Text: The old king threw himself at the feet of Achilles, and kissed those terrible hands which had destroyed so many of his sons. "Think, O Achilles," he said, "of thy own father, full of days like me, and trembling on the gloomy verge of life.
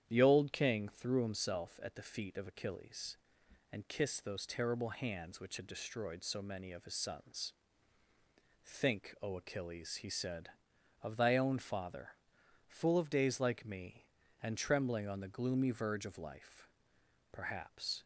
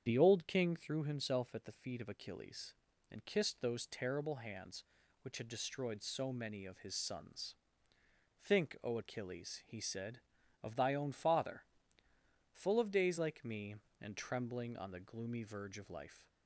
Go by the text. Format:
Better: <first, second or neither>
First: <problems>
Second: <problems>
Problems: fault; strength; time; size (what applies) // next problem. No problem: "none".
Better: second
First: starts louder than the rest; strong; until 1.0 s; 9.5 dB // goes on to say "Perhaps"; noticeable; from 17.3 s on; 0.72 s long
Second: starts louder than the rest; strong; until 1.0 s; 8 dB